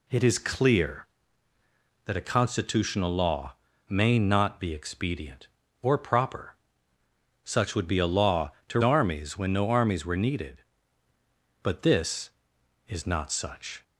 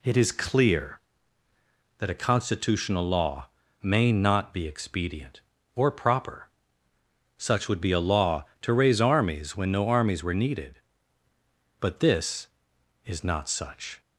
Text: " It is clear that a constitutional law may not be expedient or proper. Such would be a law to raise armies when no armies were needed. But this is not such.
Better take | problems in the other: second | pauses between "law" and "may"; slight; at 3.5 s; 0.34 s long; slight in the second // skips "raise"; at 8.8 s

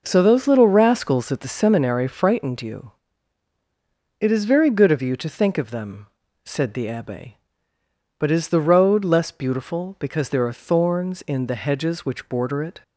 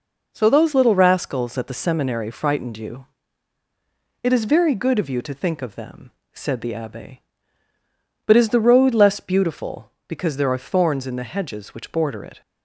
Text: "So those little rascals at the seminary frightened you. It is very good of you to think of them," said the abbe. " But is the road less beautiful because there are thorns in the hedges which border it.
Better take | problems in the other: neither | none

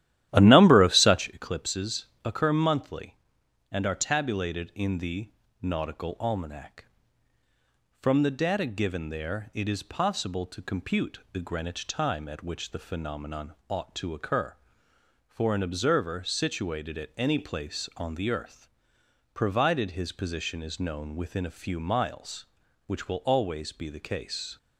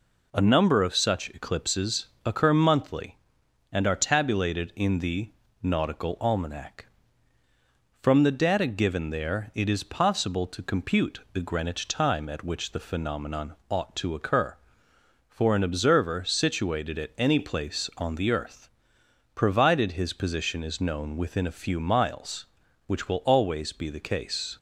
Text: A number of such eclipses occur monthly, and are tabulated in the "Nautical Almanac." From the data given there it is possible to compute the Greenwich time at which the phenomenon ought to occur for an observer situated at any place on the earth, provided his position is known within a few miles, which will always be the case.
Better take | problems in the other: second | starts louder than the rest; strong; until 1.4 s; 13 dB // pauses between "eclipses" and "occur"; slight; at 2.0 s; 0.18 s long; slight in the second // pauses between "the" and "Nautical"; slight; at 5.3 s; 0.28 s long; slight in the second

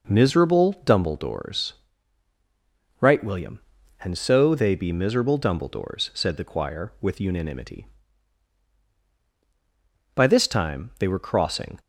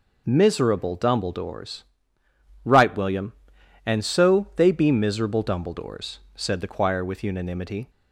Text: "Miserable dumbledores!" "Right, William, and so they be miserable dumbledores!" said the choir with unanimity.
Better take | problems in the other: second | goes on to say "By this time they were crossing"; from 10.1 s on; 1.6 s long

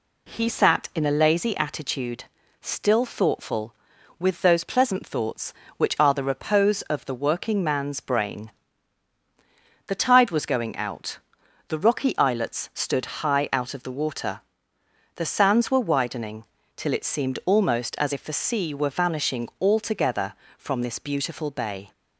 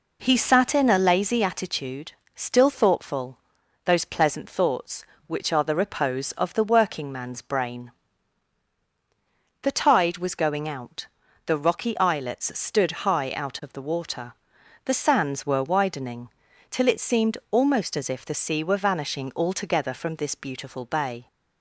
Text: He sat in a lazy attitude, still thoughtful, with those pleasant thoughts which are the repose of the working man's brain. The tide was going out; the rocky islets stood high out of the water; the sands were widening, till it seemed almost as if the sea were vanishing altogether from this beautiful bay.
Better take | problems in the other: first | skips "with"; at 3.6 s

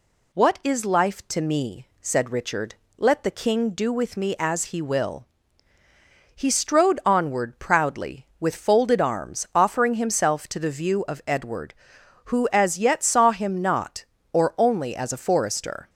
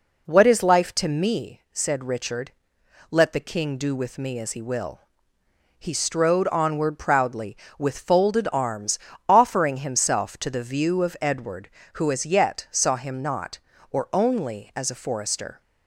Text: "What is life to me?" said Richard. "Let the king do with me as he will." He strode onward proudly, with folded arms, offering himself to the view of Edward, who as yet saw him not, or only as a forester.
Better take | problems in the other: first | starts louder than the rest; until 1.4 s; 4 dB

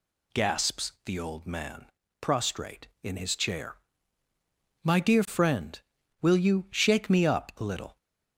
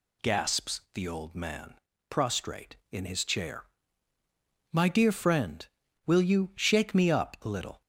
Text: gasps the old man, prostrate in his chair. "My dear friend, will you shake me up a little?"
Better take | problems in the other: neither | none

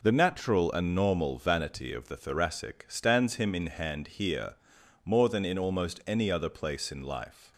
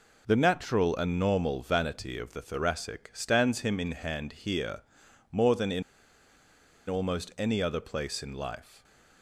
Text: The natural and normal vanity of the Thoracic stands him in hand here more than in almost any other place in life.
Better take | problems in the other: first | pauses between "here" and "more"; noticeable; at 4.8 s; 0.50 s long; noticeable in the first // pauses between "in" and "almost"; at 5.8 s; 1.0 s long // stays silent after the last word; slight; from 8.6 s on; 0.6 s long

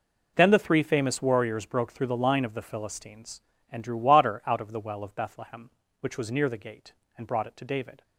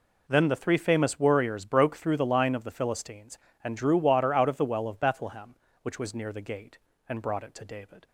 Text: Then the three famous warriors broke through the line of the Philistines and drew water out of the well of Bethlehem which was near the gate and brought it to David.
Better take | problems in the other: neither | none

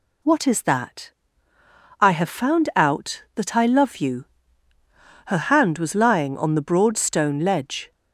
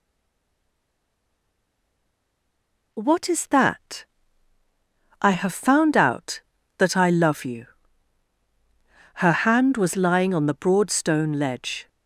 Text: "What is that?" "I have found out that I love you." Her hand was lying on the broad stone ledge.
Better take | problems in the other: first | stays silent before the first word; strong; until 2.9 s; 2.9 s long

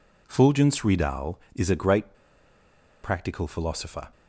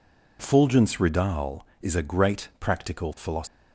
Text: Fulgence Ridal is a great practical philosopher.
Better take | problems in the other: second | pauses between "great" and "practical"; noticeable; at 2.1 s; 0.89 s long

